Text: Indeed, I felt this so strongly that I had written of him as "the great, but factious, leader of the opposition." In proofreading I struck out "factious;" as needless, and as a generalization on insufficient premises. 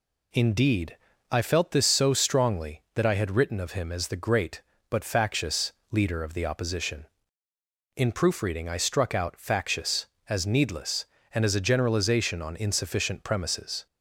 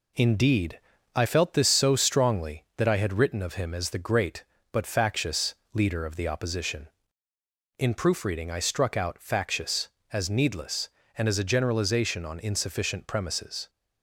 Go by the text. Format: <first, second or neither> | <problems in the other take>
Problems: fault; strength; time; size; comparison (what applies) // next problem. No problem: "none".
first | gets quieter; slight; throughout; 3 dB